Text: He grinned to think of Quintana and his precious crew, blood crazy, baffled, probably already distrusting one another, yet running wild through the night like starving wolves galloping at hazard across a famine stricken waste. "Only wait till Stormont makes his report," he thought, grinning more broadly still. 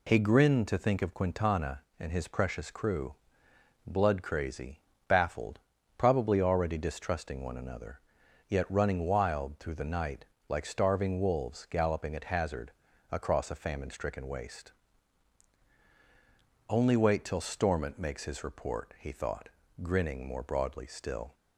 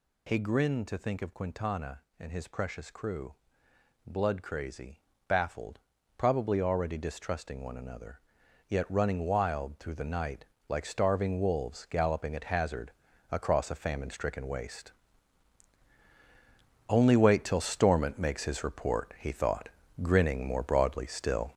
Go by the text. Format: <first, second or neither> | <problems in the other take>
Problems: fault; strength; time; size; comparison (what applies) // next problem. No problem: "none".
first | gets louder; strong; throughout; 7 dB // pauses between "night" and "like"; slight; at 10.4 s; 0.24 s long; slight in the first // pauses between "hazard" and "across"; at 12.9 s; 0.40 s long; also in the first